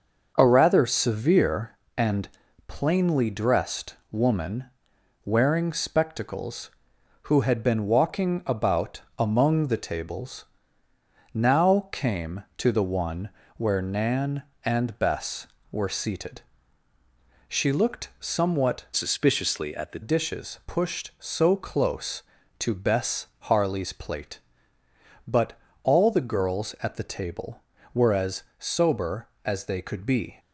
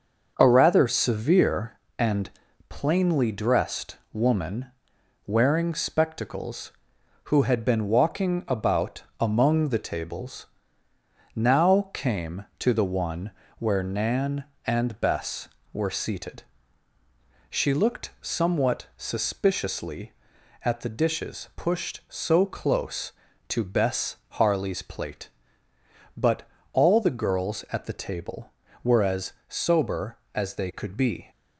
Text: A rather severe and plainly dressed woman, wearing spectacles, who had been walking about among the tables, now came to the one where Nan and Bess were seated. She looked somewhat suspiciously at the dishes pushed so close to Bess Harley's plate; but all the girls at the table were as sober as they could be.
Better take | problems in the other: second | starts louder than the rest; noticeable; until 1.3 s; 6 dB; noticeable in the second // pauses between "and" and "plainly"; at 2.2 s; 0.38 s long; also in the second // pauses between "dressed" and "woman"; slight; at 3.9 s; 0.16 s long; slight in the second // pauses between "about" and "among"; slight; at 9.0 s; 0.18 s long; slight in the second // pauses between "one" and "where"; slight; at 13.2 s; 0.28 s long; slight in the second // changes voice from "suspiciously" to "the"; from 18.9 to 20.0 s; 1.1 s long // pauses between "but" and "all"; slight; at 25.5 s; 0.30 s long; slight in the second // pauses between "as" and "sober"; slight; at 28.4 s; 0.16 s long; slight in the second

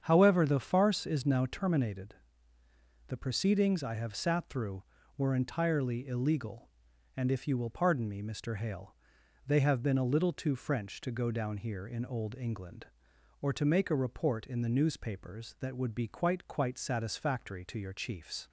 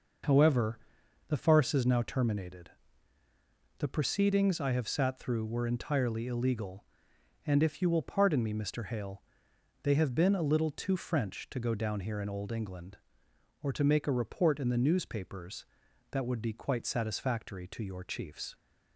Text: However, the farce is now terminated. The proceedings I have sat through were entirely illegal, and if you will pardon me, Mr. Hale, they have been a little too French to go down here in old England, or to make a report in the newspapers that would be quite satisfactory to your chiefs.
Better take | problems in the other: second | starts louder than the rest; strong; until 1.0 s; 8 dB // says "quite" twice; at 16.4 s

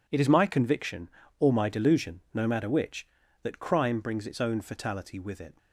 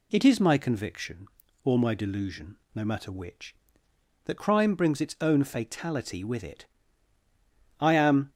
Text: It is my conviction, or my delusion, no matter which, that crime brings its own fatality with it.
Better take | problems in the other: first | goes on to say "I am"; from 7.7 s on; 0.52 s long

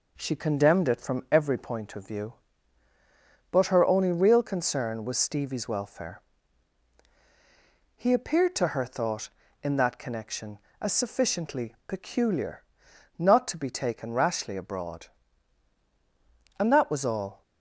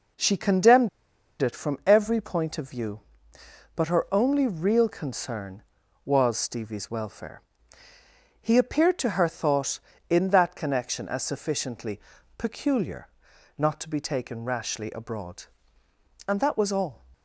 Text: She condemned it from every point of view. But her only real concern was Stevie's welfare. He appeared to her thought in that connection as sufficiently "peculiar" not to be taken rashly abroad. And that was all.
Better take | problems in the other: first | pauses between "condemned" and "it"; noticeable; at 0.8 s; 0.53 s long // pauses between "sufficiently" and "peculiar"; at 11.9 s; 0.38 s long // pauses between "peculiar" and "not"; noticeable; at 13.0 s; 0.48 s long; noticeable in the first

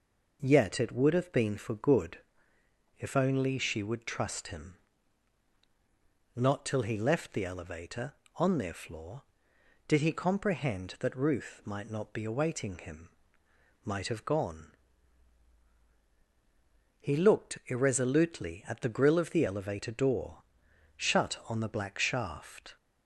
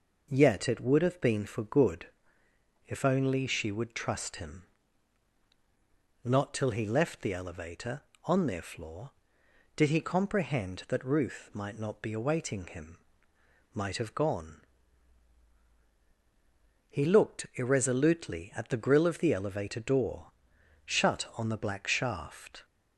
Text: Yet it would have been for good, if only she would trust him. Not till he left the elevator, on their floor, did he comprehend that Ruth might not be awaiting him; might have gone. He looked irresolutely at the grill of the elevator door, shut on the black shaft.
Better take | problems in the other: neither | none

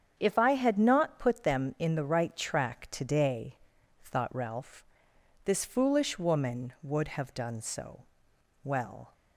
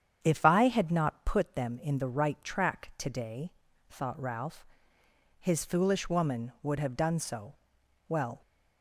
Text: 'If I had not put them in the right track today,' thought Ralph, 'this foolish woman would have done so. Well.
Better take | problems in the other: first | starts louder than the rest; strong; until 1.2 s; 8.5 dB; strong in the first // says "his" for "this"; at 5.3 s

